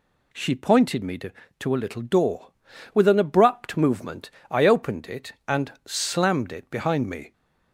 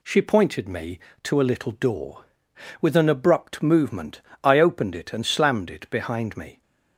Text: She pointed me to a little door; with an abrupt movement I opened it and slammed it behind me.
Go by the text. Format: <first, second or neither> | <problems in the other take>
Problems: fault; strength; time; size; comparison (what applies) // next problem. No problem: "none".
second | says "to" twice; at 1.5 s // pauses between "movement" and "I"; slight; at 4.3 s; 0.18 s long; slight in the second